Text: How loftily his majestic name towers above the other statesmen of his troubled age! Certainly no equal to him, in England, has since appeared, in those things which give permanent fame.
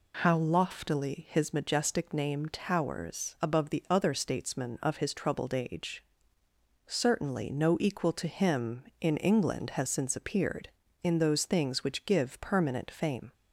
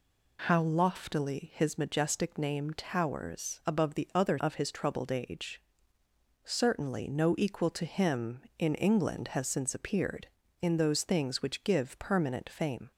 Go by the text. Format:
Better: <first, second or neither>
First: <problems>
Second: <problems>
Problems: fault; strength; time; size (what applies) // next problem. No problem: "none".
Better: first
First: none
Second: skips "statesmen"; at 4.3 s